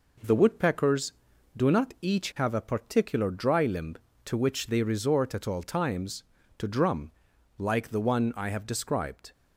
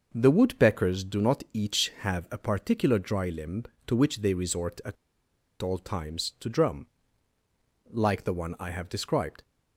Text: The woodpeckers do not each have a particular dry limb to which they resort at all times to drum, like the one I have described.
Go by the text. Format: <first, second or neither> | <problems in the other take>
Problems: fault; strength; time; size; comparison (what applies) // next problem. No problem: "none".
first | pauses between "at" and "all"; noticeable; at 4.9 s; 0.66 s long